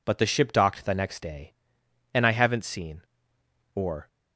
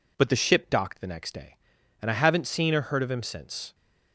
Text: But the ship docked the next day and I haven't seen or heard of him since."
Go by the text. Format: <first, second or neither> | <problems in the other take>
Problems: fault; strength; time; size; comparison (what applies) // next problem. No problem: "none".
second | stops before "heard of him since"; at 4.0 s